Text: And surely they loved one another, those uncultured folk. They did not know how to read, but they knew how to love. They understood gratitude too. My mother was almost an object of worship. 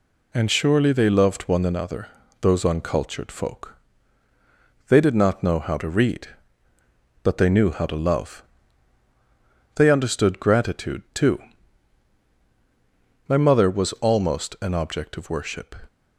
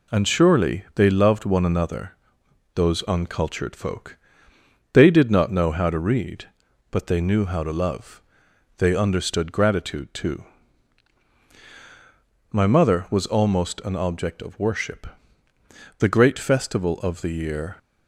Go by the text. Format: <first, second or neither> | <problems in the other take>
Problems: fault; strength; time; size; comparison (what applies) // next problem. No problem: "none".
first | goes on to say "The great festival of the year"; strong; from 15.9 s on; 1.8 s long